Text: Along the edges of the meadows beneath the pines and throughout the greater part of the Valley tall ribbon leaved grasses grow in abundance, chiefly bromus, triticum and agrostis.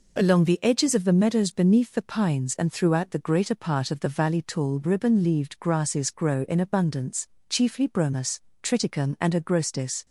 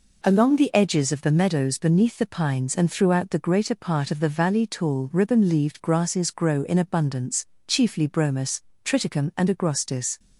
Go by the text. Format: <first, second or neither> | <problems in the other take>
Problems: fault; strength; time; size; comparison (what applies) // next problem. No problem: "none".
neither | none